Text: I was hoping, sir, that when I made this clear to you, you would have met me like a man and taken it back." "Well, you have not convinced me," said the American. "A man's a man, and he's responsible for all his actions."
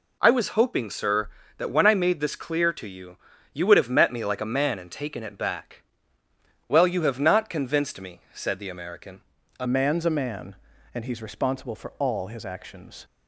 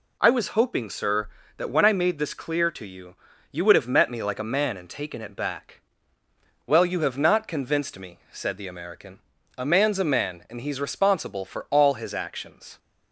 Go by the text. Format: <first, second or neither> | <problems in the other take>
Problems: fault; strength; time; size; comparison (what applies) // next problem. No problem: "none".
second | changes voice at "man's"; from 9.6 s on; 3.4 s long